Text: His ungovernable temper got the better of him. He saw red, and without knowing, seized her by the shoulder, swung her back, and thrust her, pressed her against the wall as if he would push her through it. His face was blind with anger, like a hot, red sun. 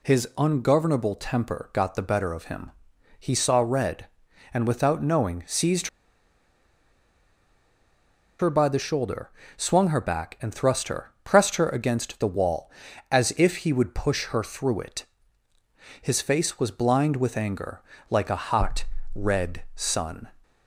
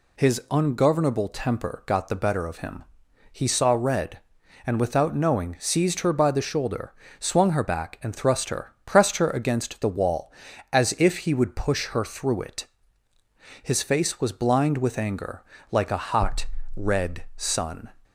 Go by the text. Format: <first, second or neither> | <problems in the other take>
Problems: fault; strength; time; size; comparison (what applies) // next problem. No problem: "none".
second | pauses between "seized" and "her"; strong; at 5.8 s; 2.5 s long